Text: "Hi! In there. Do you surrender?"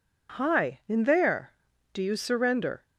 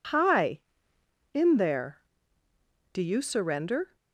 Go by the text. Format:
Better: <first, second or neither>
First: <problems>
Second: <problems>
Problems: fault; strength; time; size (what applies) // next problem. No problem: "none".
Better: neither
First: none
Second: none